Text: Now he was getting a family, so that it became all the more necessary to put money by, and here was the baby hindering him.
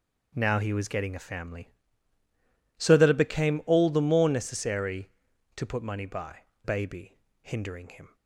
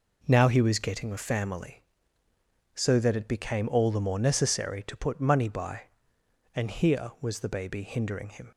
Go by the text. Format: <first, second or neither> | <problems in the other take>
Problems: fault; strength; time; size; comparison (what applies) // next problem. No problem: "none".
second | skips "and here was the"; at 6.5 s // pauses between "baby" and "hindering"; slight; at 7.1 s; 0.26 s long